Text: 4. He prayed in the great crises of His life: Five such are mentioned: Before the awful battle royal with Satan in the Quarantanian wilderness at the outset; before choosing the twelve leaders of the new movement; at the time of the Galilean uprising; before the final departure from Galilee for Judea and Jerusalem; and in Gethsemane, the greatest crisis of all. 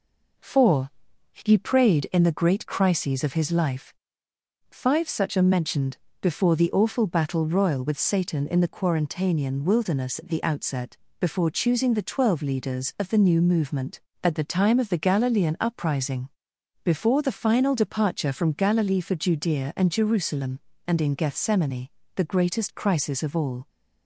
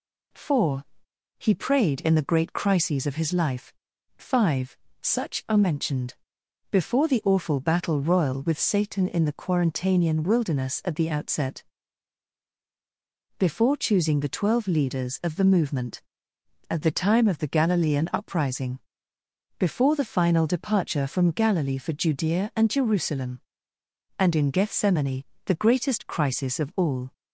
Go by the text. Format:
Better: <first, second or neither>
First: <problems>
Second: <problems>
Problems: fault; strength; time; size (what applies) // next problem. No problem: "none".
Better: first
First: none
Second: pauses between "Five" and "such"; slight; at 4.7 s; 0.24 s long // skips "new"; at 15.4 s